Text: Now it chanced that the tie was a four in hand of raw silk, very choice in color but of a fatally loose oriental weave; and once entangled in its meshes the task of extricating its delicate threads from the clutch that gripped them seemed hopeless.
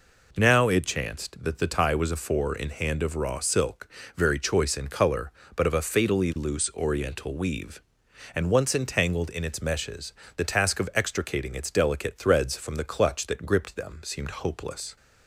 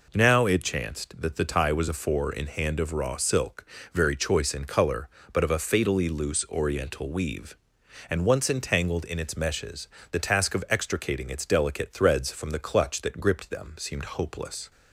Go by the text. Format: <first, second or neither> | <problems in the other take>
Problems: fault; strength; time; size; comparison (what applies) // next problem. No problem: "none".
neither | pauses between "meshes" and "the"; slight; the same in both